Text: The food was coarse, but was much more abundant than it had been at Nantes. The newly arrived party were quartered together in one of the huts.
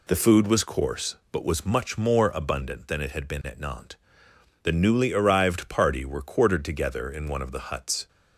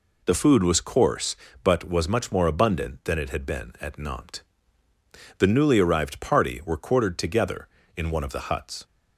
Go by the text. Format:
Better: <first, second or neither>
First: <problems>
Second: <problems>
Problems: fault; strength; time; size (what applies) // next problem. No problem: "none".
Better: neither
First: none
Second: none